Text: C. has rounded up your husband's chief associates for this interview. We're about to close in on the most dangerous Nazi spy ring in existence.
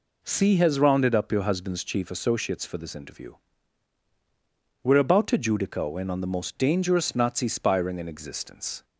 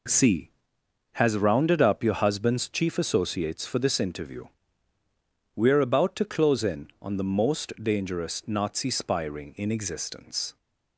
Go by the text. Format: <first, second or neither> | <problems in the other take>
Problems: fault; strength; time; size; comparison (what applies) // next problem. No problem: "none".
second | says "judico" for "close"; at 5.3 s